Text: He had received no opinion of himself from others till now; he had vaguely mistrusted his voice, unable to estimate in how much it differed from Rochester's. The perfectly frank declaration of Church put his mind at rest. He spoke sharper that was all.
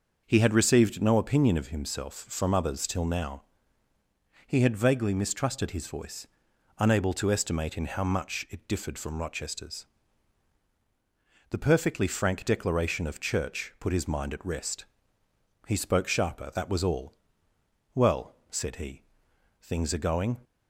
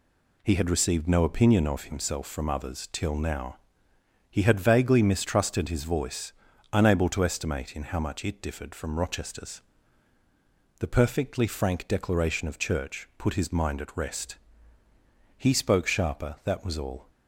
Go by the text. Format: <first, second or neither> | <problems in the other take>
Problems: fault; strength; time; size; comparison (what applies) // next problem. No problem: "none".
second | starts louder than the rest; until 1.2 s; 6.5 dB // goes on to say "Well said he Things are going"; strong; from 17.9 s on; 2.4 s long